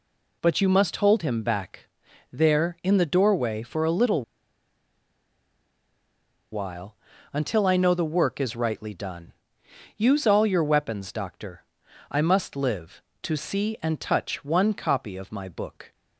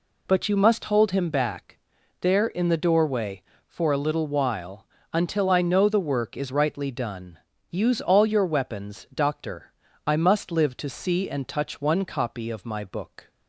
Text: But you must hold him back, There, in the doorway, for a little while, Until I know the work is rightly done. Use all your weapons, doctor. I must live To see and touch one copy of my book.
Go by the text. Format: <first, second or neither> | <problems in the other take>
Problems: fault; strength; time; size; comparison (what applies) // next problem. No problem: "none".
second | pauses between "little" and "while"; strong; at 4.2 s; 2.3 s long